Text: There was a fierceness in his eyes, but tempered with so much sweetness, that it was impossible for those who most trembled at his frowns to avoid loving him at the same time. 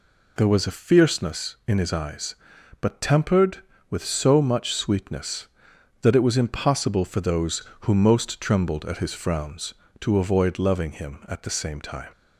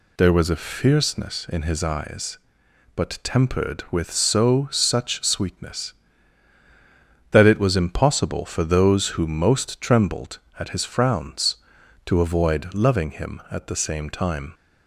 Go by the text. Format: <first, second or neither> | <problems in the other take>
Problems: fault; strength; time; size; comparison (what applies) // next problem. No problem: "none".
first | says "such" for "much"; at 4.6 s